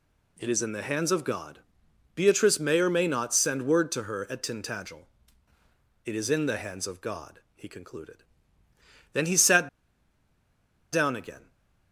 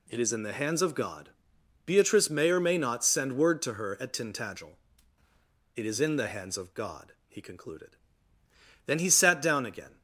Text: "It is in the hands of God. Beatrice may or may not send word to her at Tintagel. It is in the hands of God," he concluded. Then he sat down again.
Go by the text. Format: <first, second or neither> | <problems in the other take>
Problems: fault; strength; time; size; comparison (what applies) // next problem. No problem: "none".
second | pauses between "sat" and "down"; strong; at 9.6 s; 1.2 s long